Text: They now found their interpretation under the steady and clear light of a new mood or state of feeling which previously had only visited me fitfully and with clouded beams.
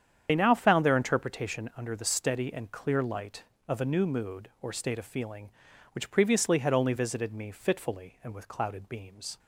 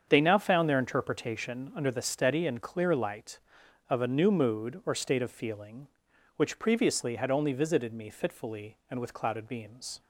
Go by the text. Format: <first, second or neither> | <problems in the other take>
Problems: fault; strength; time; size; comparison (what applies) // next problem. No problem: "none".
second | loses the start of "They"; at 0.2 s; 60 ms // starts louder than the rest; strong; until 1.3 s; 8.5 dB; strong in the second